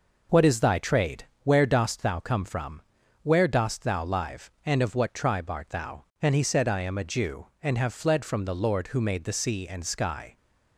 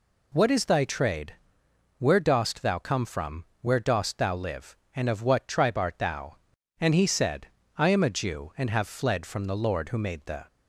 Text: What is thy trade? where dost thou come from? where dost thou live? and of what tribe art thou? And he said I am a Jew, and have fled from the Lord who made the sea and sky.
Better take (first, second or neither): first